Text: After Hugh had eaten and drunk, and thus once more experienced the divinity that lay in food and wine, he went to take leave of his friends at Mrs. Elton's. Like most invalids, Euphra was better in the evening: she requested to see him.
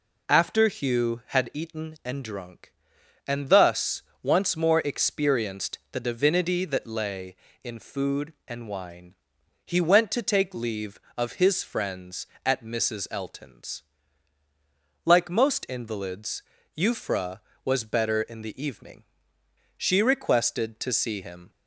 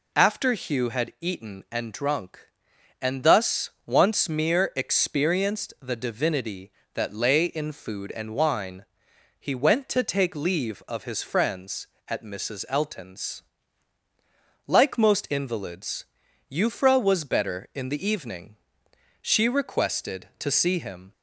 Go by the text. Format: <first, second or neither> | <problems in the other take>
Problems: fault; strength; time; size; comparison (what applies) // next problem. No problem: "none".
first | pauses between "thus" and "once"; slight; at 3.7 s; 0.16 s long; slight in the first // says "mere" for "more"; at 4.2 s